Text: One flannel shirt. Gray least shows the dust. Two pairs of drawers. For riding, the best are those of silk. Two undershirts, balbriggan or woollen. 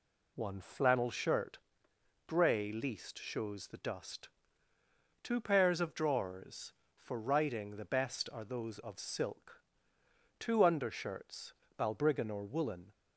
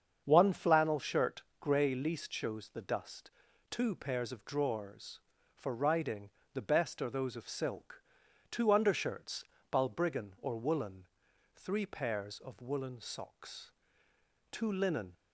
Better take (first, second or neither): first